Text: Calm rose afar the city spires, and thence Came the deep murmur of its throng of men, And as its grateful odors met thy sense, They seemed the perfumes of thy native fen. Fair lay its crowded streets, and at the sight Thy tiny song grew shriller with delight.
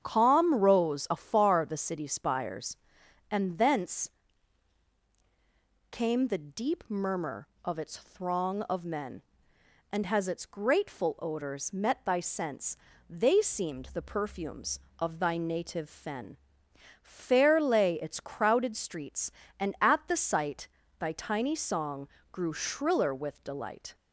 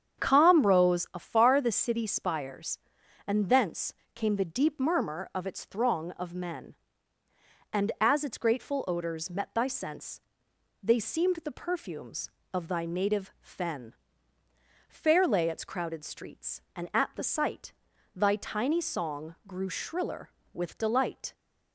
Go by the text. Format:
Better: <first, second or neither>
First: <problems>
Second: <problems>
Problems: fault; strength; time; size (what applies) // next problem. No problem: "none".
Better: second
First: starts louder than the rest; strong; until 1.0 s; 8 dB // pauses between "thence" and "Came"; strong; at 4.1 s; 1.8 s long // says "has" for "as"; at 10.0 s // pauses between "sight" and "Thy"; slight; at 20.6 s; 0.30 s long // pauses between "song" and "grew"; slight; at 22.0 s; 0.24 s long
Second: starts louder than the rest; strong; until 1.2 s; 8 dB // pauses between "thence" and "Came"; slight; at 3.9 s; 0.22 s long // pauses between "sight" and "Thy"; at 17.7 s; 0.40 s long